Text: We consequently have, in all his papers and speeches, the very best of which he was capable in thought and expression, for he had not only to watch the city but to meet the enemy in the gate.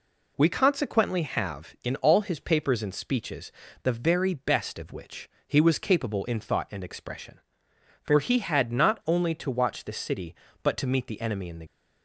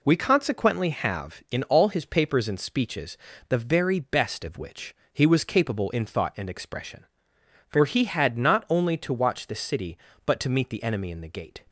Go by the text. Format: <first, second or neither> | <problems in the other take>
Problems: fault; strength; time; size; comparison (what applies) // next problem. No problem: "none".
second | pauses between "which" and "he"; slight; at 5.2 s; 0.18 s long; slight in the second // stops before "gate"; at 11.6 s